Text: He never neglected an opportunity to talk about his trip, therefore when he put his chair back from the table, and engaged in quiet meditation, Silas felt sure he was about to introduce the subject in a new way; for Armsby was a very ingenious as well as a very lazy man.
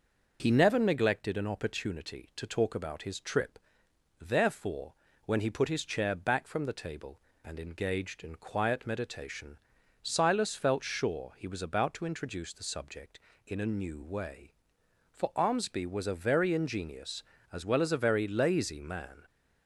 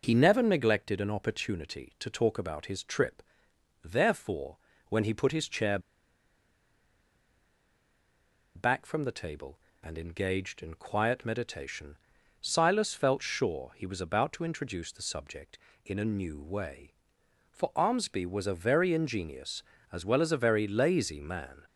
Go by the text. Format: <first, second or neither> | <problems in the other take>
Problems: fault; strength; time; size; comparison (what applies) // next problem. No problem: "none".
first | pauses between "therefore" and "when"; slight; at 4.5 s; 0.32 s long; slight in the first // pauses between "chair" and "back"; strong; at 5.7 s; 2.7 s long